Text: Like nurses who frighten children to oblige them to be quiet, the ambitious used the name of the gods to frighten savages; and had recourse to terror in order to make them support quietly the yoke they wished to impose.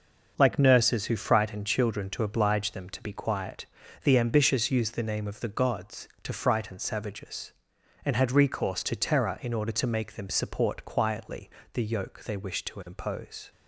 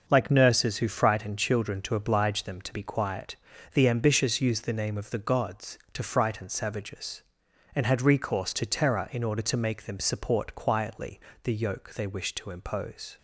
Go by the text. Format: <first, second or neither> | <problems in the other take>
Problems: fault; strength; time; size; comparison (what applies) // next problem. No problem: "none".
neither | starts louder than the rest; noticeable; the same in both // pauses between "quietly" and "the"; slight; the same in both